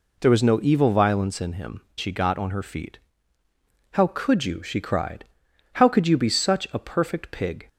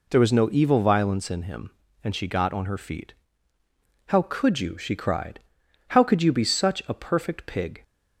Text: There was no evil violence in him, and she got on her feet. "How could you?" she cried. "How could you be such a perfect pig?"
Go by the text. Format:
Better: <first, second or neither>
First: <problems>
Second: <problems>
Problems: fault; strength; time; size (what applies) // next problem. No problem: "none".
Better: second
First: skips "and"; at 1.9 s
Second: none